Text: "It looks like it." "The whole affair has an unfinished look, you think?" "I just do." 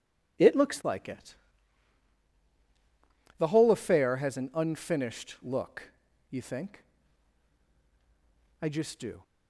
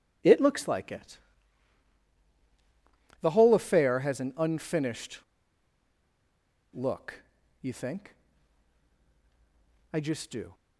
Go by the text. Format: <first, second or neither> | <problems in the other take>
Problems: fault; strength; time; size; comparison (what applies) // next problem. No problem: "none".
first | pauses between "unfinished" and "look"; strong; at 5.1 s; 1.5 s long